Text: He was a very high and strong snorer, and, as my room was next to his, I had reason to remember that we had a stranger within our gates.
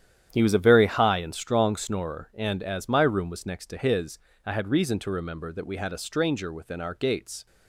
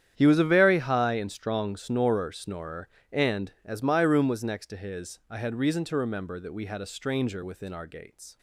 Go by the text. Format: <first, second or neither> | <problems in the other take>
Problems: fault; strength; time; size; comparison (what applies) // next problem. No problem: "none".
first | starts louder than the rest; strong; until 1.1 s; 9.5 dB; strong in the first // says "snorer" twice; at 2.3 s